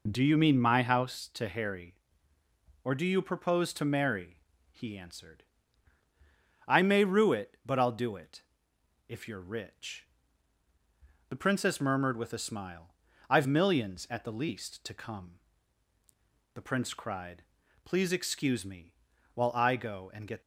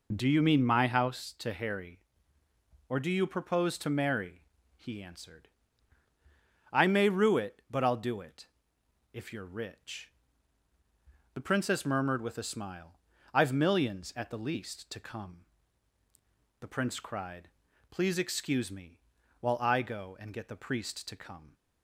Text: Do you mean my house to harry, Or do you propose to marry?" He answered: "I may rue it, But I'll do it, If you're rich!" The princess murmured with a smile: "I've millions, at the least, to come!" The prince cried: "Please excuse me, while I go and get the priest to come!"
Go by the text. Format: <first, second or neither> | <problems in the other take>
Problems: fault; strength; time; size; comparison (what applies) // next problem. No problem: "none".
second | stops before "the priest to come"; at 20.4 s